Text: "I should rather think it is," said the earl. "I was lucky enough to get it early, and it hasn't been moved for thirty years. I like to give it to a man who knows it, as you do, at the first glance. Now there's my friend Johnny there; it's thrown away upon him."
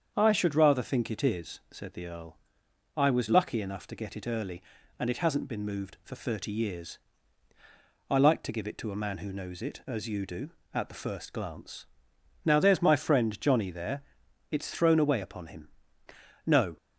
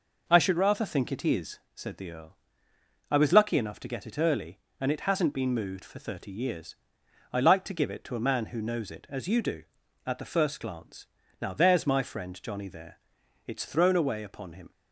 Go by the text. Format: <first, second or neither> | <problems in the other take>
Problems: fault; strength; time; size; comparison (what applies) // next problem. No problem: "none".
second | starts louder than the rest; strong; until 1.1 s; 7.5 dB // goes on to say "No"; slight; from 16.4 s on; 0.32 s long